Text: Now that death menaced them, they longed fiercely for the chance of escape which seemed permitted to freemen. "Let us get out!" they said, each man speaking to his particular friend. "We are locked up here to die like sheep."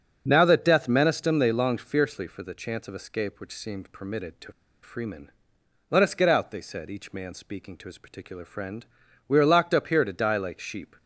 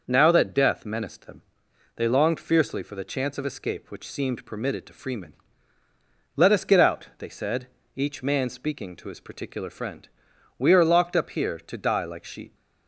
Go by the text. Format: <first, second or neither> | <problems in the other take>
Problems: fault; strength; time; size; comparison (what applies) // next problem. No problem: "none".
second | starts louder than the rest; until 1.3 s; 7 dB // pauses between "to" and "freemen"; slight; at 4.5 s; 0.32 s long